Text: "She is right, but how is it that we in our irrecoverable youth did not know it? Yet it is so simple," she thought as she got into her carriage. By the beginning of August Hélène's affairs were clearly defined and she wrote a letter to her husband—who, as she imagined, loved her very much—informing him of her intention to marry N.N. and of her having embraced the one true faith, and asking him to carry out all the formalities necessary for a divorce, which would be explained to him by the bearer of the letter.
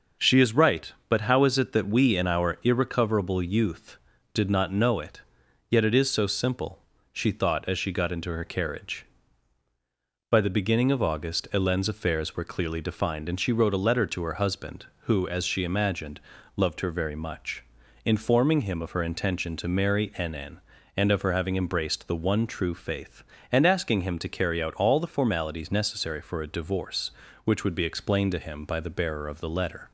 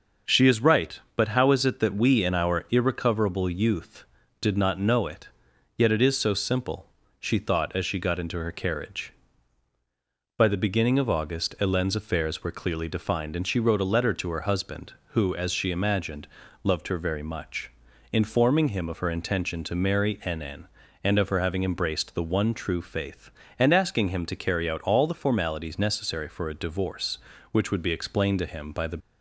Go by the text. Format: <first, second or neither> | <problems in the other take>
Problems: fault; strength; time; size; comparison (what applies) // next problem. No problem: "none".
first | starts louder than the rest; until 1.4 s; 6 dB; also in the first // stops before "bearer of the letter"; at 28.9 s